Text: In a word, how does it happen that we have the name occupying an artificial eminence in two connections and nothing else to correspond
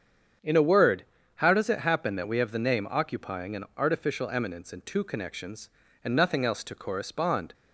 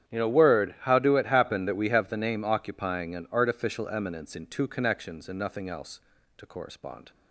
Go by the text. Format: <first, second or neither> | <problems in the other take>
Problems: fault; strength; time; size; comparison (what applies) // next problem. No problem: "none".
first | starts louder than the rest; strong; until 1.1 s; 9.5 dB; strong in the first // says "do" for "does"; at 1.0 s